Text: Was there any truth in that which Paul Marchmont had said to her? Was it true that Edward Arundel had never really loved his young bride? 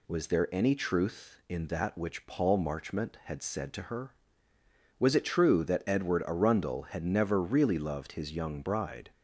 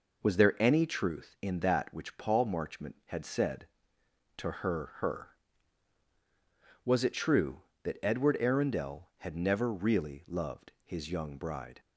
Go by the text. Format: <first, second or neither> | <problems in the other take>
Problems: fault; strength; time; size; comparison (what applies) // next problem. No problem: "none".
first | says "her" twice; at 4.9 s